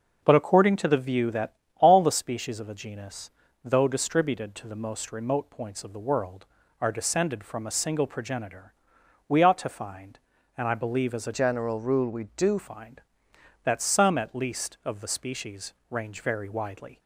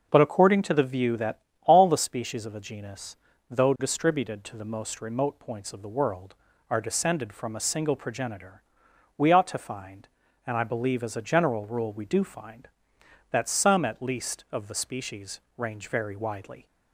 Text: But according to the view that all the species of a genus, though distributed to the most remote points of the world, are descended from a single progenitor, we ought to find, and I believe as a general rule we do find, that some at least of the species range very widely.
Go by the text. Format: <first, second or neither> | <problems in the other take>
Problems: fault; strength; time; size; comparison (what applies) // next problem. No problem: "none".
second | starts louder than the rest; noticeable; until 1.2 s; 6 dB; noticeable in the second // pauses between "that" and "all"; slight; at 1.5 s; 0.22 s long; slight in the second // changes voice from "general" to "do"; from 11.3 to 12.5 s; 1.2 s long // pauses between "species" and "range"; slight; at 15.7 s; 0.16 s long; slight in the second